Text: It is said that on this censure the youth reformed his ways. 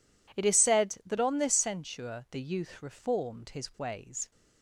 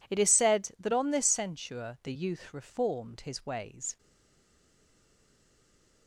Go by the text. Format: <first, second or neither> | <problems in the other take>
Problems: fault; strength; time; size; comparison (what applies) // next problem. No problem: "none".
first | stays silent after the last word; from 3.9 s on; 2.1 s long